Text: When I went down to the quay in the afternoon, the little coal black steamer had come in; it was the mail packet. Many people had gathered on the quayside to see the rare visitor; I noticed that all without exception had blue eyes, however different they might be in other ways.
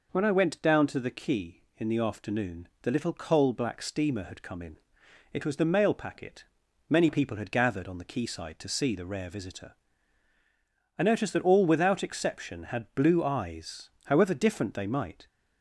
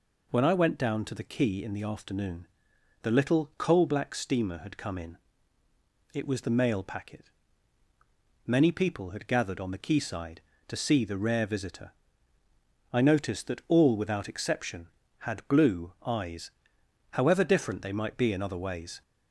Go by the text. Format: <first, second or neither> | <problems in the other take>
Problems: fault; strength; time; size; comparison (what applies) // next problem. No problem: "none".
second | stops before "be in other ways"; at 15.2 s